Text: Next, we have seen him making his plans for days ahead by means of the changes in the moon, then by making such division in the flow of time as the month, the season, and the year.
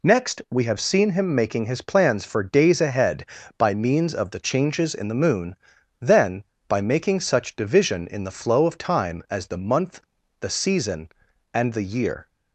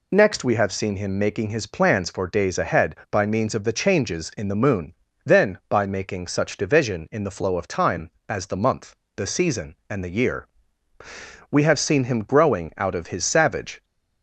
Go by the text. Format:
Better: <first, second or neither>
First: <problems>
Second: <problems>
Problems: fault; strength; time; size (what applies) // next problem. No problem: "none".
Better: first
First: none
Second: goes on to say "We have seen him growing out of his savage"; strong; from 11.5 s on; 2.3 s long